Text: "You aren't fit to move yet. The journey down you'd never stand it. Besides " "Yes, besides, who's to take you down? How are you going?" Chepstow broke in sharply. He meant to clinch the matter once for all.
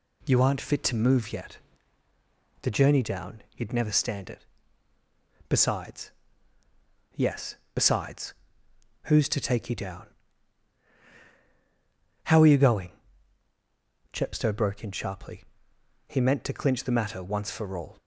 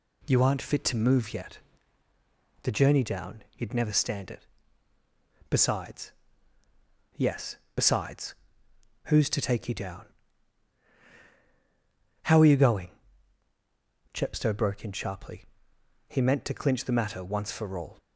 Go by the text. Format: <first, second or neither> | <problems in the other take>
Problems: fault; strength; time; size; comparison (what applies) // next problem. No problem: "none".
neither | none